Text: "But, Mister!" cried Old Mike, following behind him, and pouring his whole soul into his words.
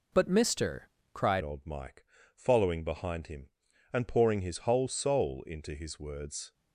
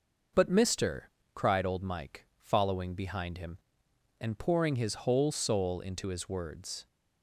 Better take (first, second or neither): second